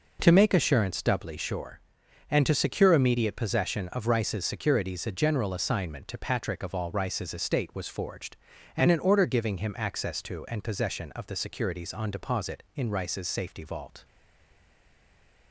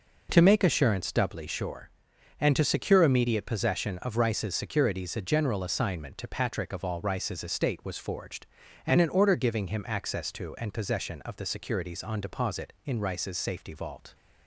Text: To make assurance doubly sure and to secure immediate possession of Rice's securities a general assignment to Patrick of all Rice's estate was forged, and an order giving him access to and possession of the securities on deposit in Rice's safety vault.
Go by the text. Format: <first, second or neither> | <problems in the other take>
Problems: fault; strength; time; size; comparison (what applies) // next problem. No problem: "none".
second | stays silent after the last word; noticeable; from 14.0 s on; 1.5 s long